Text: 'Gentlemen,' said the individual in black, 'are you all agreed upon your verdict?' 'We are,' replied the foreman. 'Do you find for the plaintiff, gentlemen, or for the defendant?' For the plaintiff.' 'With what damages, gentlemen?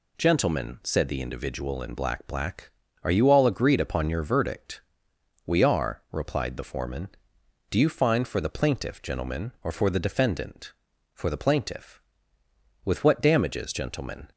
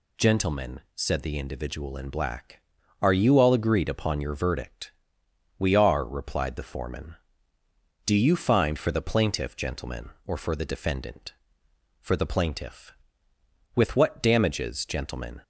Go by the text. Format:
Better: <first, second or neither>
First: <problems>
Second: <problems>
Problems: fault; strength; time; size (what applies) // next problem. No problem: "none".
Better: second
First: says "black" twice; at 2.2 s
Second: none